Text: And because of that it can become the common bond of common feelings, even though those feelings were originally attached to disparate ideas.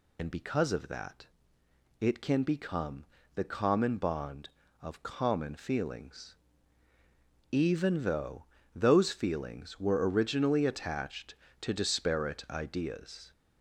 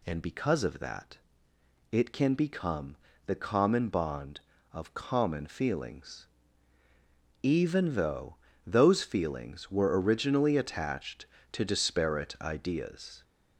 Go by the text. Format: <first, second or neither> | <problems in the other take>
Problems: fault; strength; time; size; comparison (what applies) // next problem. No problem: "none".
second | loses the start of "And"; at 0.1 s; 85 ms // pauses between "that" and "it"; noticeable; at 1.2 s; 0.74 s long; noticeable in the second // pauses between "become" and "the"; slight; at 3.0 s; 0.28 s long; slight in the second // pauses between "though" and "those"; slight; at 8.4 s; 0.30 s long; slight in the second